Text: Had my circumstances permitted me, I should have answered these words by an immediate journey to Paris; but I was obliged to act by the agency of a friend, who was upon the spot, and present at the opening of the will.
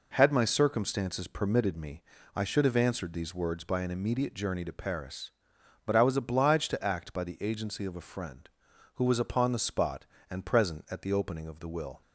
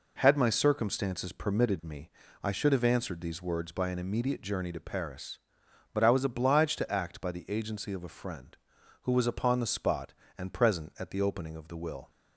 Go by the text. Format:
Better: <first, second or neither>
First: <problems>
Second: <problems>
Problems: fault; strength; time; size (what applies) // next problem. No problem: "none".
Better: neither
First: none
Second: none